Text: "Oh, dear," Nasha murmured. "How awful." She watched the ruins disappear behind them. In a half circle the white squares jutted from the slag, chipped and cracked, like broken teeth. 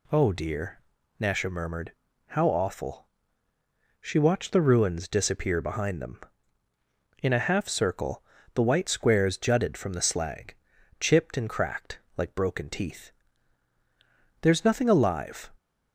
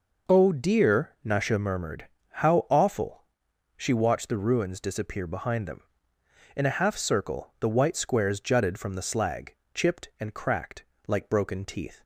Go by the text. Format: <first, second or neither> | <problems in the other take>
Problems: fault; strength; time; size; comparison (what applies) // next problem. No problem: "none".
second | pauses between "circle" and "the"; slight; at 8.2 s; 0.30 s long // goes on to say "There's nothing alive"; noticeable; from 14.4 s on; 1.0 s long